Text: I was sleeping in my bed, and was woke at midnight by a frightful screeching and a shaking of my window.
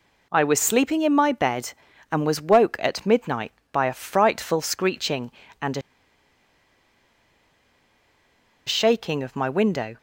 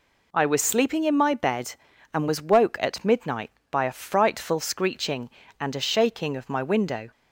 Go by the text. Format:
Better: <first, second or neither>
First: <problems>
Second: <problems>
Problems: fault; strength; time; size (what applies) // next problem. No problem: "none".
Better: second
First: pauses between "a" and "shaking"; strong; at 5.8 s; 2.8 s long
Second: none